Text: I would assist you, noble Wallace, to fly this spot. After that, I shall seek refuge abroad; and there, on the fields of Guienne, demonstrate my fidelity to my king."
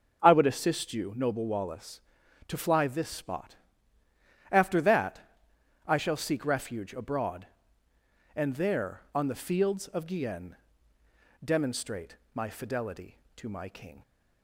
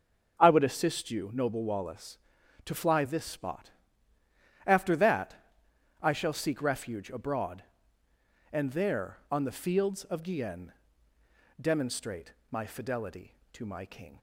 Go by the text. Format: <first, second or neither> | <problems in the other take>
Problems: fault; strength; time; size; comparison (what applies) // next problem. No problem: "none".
neither | starts louder than the rest; the same in both // pauses between "demonstrate" and "my"; slight; the same in both